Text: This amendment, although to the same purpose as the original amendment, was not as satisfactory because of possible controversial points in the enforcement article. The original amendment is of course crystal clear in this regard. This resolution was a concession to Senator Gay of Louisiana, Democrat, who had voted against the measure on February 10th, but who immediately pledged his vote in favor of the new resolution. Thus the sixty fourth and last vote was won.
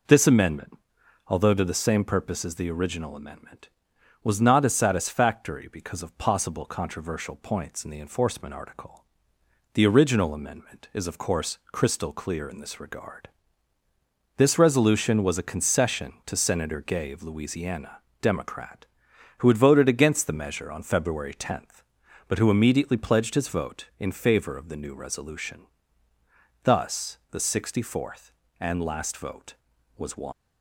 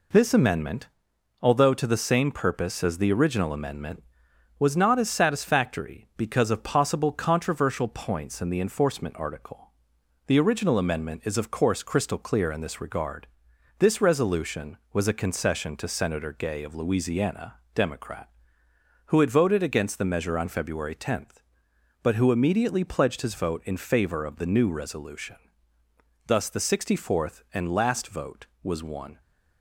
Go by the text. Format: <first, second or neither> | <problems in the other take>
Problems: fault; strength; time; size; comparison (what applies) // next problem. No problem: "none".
second | leaves "won" unfinished; at 30.3 s; 90 ms